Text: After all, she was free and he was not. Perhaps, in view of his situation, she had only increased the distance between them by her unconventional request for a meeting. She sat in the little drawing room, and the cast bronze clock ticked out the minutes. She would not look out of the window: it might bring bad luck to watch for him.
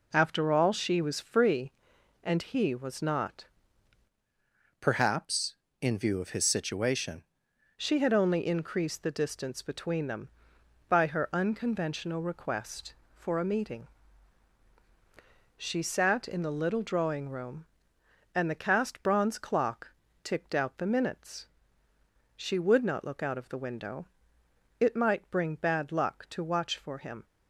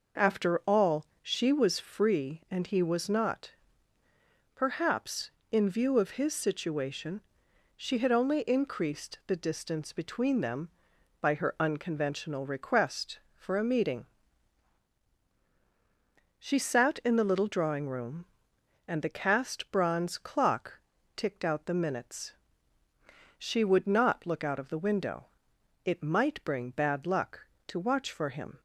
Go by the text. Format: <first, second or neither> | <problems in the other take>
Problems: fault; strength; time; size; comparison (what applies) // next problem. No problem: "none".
second | changes voice from "Perhaps" to "situation"; from 4.7 to 7.2 s; 2.5 s long // pauses between "clock" and "ticked"; slight; at 19.9 s; 0.32 s long; also in the second